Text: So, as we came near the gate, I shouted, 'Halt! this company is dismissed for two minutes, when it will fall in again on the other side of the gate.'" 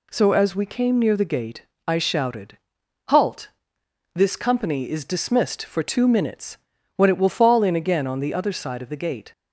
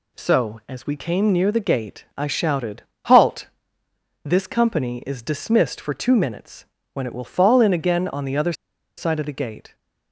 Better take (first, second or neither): first